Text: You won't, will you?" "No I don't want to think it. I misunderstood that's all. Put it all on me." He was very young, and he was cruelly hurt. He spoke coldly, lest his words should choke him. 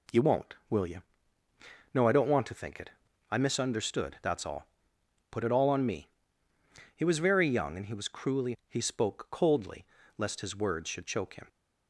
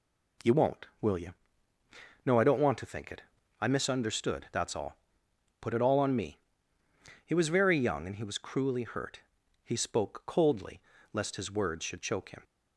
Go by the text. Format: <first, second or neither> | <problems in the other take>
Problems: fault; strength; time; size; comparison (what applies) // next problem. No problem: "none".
second | skips "hurt"; at 8.6 s